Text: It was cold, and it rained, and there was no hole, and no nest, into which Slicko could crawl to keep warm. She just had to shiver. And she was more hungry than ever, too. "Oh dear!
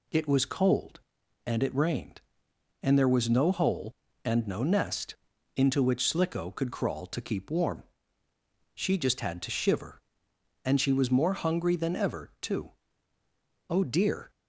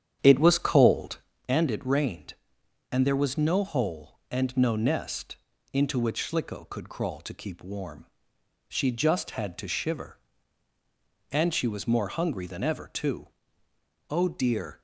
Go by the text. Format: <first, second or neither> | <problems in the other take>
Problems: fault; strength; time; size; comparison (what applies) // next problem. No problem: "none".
first | starts louder than the rest; strong; until 1.4 s; 9 dB